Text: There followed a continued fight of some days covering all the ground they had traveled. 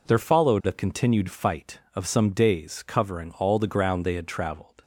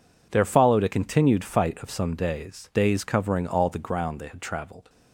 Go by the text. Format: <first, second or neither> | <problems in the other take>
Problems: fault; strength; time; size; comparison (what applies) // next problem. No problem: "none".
first | says "days" twice; at 2.7 s